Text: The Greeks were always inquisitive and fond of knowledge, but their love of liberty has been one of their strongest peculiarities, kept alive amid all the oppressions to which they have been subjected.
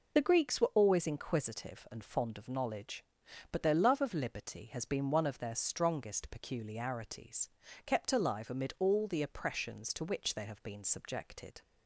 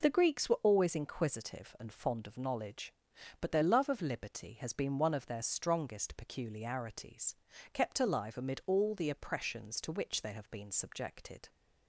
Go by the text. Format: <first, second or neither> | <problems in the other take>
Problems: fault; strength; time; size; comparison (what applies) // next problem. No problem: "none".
second | loses the start of "The"; at 0.1 s; 35 ms